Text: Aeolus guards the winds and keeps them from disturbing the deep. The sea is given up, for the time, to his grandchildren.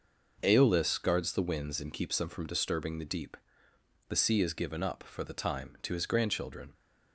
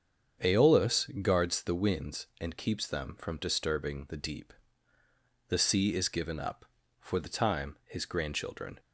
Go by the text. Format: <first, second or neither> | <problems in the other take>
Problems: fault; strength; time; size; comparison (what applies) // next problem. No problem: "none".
first | starts louder than the rest; strong; until 1.6 s; 7.5 dB // pauses between "Aeolus" and "guards"; slight; at 1.0 s; 0.16 s long // skips "to"; at 7.8 s